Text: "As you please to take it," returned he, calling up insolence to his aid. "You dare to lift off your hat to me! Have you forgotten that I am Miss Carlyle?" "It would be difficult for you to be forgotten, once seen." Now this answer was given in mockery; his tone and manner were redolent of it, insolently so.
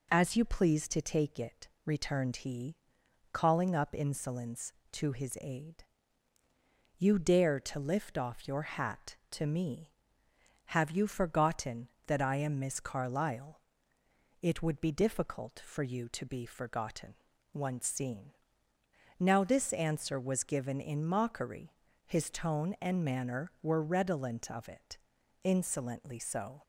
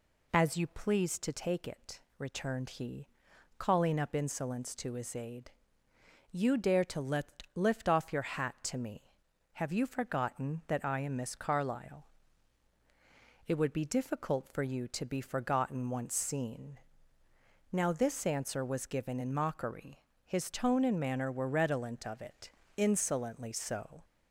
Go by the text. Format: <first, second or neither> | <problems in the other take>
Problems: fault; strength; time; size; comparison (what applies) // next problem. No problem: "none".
first | says "lift" twice; at 7.5 s